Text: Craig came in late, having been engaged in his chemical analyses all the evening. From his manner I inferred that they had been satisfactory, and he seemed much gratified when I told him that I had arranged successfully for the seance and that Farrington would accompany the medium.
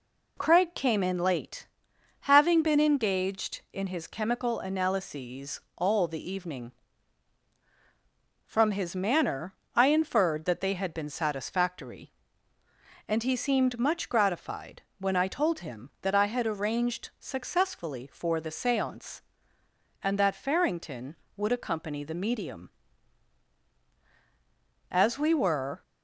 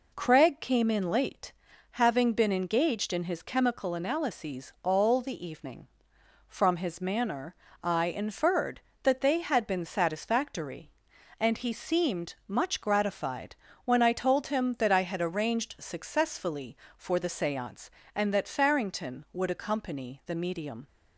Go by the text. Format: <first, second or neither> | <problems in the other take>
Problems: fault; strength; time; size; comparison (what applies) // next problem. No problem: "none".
second | pauses between "analyses" and "all"; slight; at 5.5 s; 0.16 s long // pauses between "manner" and "I"; slight; at 9.5 s; 0.20 s long; slight in the second // pauses between "gratified" and "when"; slight; at 14.8 s; 0.18 s long; slight in the second // goes on to say "As we were"; noticeable; from 24.9 s on; 0.90 s long